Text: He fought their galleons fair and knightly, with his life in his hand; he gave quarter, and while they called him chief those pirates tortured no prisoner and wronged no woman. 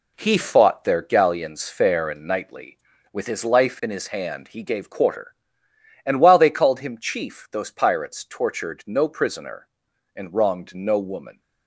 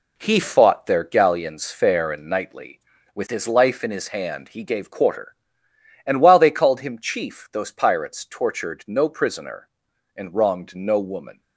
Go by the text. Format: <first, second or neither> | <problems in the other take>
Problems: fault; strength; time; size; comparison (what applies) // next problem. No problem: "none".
neither | none